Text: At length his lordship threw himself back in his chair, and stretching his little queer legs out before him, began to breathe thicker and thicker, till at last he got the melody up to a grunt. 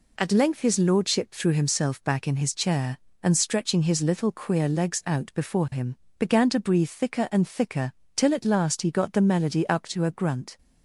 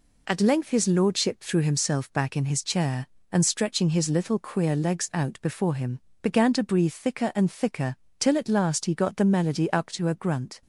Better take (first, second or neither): neither